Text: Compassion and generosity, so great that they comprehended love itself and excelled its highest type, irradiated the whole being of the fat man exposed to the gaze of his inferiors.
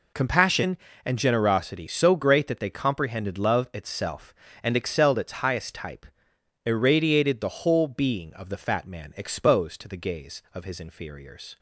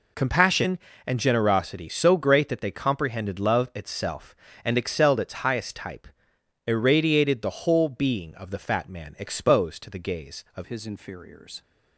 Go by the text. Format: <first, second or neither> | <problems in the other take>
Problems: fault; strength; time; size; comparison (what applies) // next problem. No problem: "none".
first | changes voice at "his"; from 10.6 s on; 1.0 s long